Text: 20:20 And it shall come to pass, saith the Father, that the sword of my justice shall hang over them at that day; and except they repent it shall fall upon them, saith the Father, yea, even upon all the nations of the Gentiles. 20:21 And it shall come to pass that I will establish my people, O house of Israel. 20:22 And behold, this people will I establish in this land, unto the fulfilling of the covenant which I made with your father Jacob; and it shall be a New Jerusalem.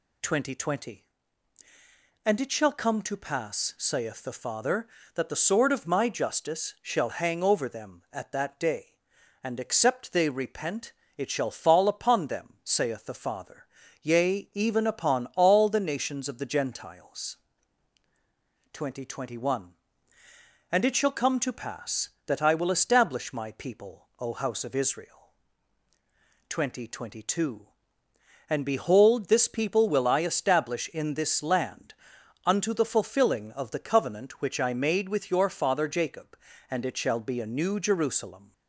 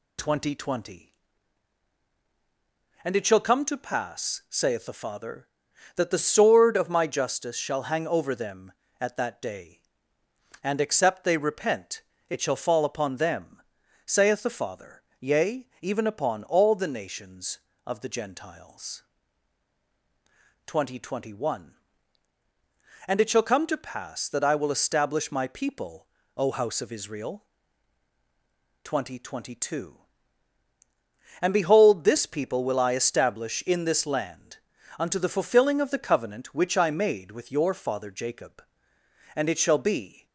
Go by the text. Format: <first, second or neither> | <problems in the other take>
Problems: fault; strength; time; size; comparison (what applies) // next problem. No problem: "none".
first | pauses between "repent" and "it"; slight; at 12.0 s; 0.26 s long; slight in the first // stops before "a New Jerusalem"; at 40.2 s